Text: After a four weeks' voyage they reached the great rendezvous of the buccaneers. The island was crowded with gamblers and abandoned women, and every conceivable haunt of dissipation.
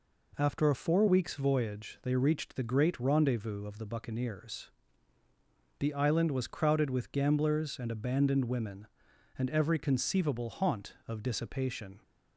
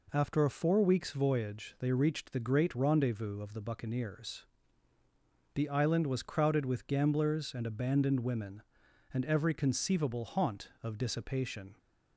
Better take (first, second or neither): neither